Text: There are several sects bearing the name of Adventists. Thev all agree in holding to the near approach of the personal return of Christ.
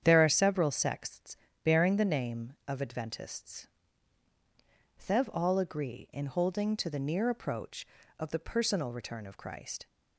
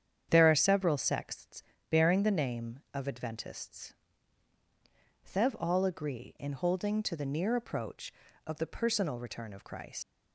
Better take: first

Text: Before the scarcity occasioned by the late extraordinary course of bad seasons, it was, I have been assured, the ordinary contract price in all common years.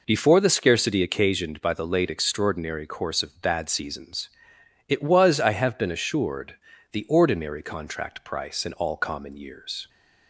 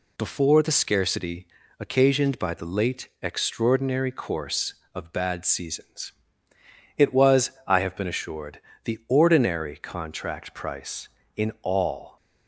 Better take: first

